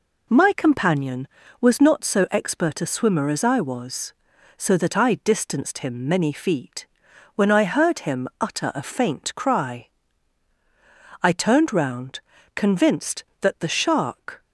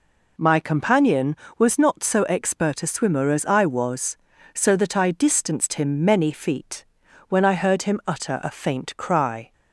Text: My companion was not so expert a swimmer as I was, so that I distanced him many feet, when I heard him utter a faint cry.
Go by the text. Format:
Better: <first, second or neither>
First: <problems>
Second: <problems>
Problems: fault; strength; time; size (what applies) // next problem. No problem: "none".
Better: second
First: goes on to say "I turned round convinced that the shark"; strong; from 11.2 s on; 3.2 s long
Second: none